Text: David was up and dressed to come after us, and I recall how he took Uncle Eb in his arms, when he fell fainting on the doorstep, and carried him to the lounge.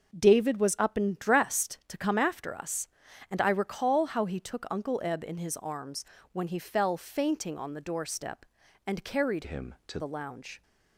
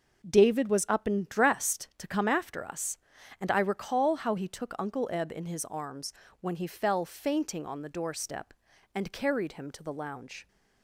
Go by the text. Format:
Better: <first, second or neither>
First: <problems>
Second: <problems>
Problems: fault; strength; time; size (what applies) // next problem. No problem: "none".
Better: second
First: changes voice from "him" to "to"; from 9.4 to 9.9 s; 0.5 s long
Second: none